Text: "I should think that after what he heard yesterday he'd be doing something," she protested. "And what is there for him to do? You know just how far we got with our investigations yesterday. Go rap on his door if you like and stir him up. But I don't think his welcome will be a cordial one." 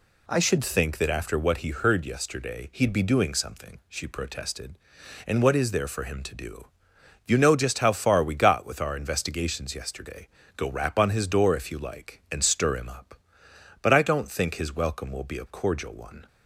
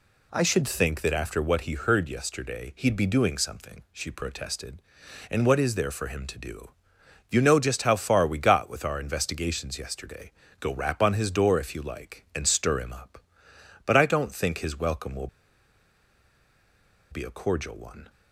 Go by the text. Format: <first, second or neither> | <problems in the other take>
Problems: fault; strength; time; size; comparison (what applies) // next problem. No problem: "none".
first | pauses between "will" and "be"; strong; at 15.2 s; 1.8 s long